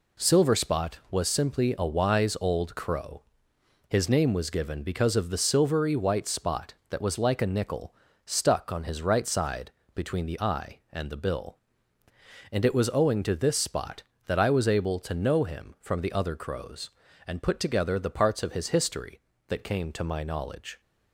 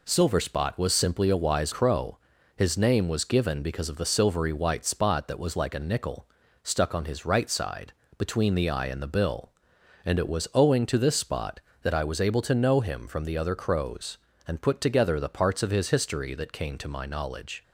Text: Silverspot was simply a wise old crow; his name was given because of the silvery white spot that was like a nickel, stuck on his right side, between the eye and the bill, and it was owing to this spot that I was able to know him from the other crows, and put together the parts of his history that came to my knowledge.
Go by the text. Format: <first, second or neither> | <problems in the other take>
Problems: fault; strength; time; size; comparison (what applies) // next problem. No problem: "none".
first | skips "old"; at 1.7 s